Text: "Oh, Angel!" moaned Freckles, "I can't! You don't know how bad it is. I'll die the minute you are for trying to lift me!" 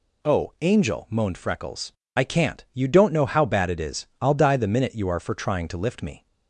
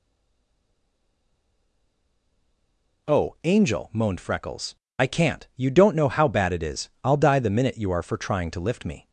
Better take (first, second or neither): first